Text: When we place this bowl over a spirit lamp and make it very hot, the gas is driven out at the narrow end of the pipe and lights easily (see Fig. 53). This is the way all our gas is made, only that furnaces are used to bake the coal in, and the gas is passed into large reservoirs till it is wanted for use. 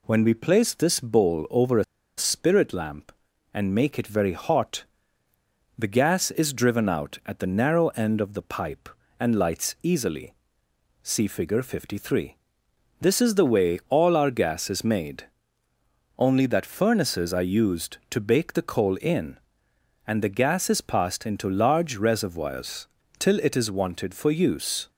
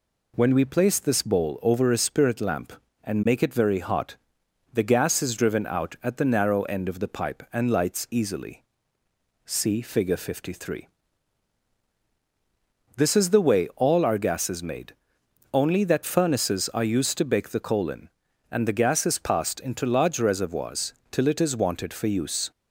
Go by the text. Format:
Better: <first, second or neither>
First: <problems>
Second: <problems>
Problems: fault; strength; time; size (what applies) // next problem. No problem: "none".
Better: second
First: pauses between "a" and "spirit"; slight; at 1.8 s; 0.33 s long // pauses between "reservoirs" and "till"; slight; at 22.8 s; 0.32 s long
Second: pauses between "reservoirs" and "till"; slight; at 20.9 s; 0.18 s long